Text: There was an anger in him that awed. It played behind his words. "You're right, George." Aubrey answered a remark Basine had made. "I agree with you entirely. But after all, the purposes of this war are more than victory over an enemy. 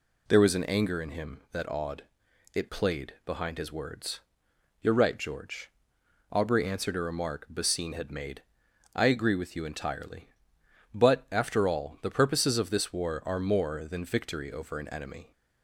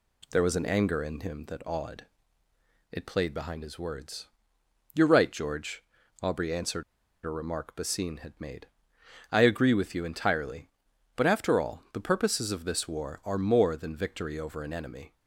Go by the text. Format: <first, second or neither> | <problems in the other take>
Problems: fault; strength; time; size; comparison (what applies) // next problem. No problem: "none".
first | pauses between "answered" and "a"; at 6.8 s; 0.41 s long